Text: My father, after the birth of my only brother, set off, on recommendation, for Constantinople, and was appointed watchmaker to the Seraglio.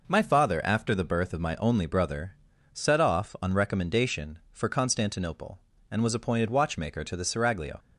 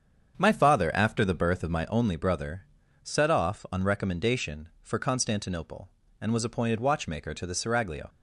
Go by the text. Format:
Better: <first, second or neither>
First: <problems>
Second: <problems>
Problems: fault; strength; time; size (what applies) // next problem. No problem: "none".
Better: first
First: none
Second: starts louder than the rest; strong; until 1.9 s; 7.5 dB